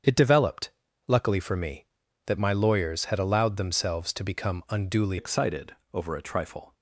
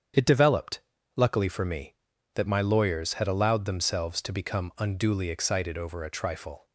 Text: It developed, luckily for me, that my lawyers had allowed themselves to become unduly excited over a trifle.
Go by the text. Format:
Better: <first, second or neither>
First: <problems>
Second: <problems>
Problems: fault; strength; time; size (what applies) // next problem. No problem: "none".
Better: second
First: starts louder than the rest; strong; until 1.4 s; 8 dB // changes voice at "excited"; from 5.1 s on; 1.6 s long // pauses between "excited" and "over"; slight; at 5.7 s; 0.18 s long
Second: starts louder than the rest; strong; until 1.5 s; 8 dB